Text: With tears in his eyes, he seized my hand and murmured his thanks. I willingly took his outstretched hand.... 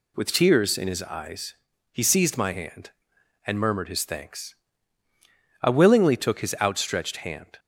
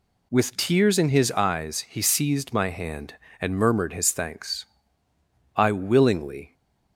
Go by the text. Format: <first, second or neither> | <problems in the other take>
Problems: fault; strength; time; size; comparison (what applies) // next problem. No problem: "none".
first | stops before "took his outstretched hand"; at 6.5 s